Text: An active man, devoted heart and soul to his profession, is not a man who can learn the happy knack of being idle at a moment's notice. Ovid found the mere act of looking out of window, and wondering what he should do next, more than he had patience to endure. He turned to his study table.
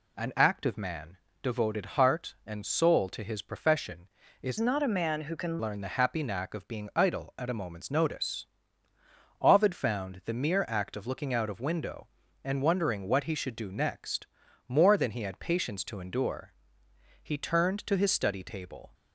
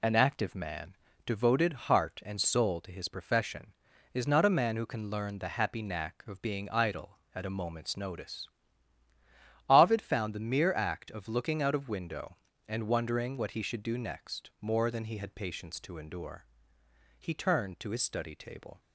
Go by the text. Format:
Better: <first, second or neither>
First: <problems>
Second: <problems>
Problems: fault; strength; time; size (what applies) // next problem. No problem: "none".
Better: second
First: changes voice from "not" to "can"; from 4.6 to 5.5 s; 0.9 s long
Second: none